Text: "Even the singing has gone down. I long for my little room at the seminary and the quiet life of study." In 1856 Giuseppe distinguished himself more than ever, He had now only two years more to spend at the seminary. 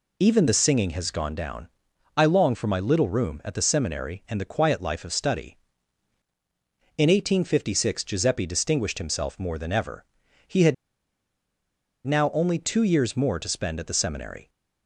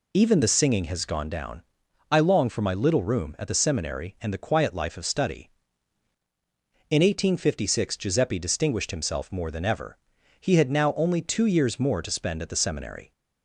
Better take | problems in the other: second | pauses between "had" and "now"; strong; at 10.7 s; 1.3 s long

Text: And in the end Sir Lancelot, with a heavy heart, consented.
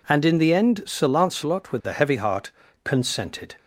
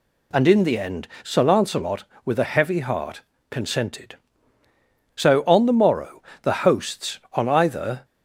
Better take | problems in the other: first | pauses between "end" and "Sir"; slight; at 1.0 s; 0.16 s long // goes on to say "So on the morrow the hosts on either"; strong; from 5.1 s on; 2.8 s long

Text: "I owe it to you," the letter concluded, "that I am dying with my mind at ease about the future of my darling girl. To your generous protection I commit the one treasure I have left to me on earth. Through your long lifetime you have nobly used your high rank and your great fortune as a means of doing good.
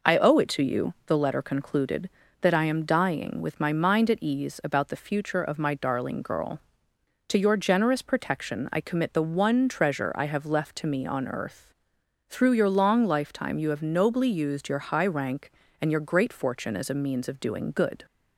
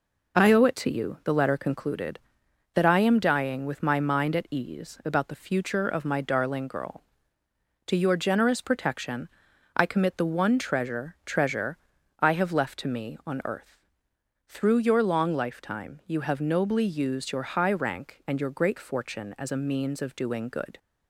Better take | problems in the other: first | pauses between "protection" and "I"; noticeable; at 9.2 s; 0.48 s long // says "treasure" twice; at 11.2 s

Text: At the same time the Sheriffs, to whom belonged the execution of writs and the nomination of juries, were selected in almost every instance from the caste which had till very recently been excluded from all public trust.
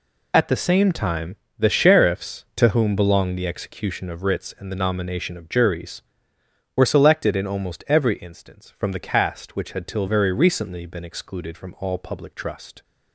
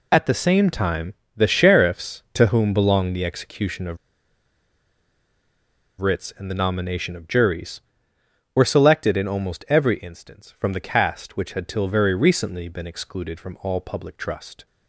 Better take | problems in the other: first | pauses between "time" and "the"; slight; at 1.1 s; 0.22 s long; slight in the first // pauses between "of" and "writs"; strong; at 3.9 s; 2.0 s long

